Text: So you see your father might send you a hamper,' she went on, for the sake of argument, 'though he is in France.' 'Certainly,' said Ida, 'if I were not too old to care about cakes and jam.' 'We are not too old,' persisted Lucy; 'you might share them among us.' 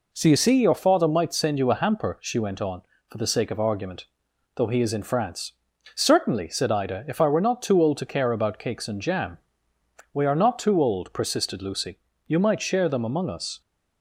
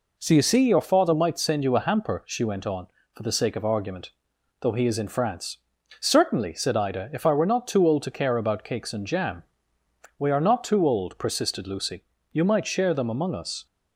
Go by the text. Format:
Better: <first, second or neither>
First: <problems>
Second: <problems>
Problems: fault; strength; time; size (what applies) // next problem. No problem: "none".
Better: neither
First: none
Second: none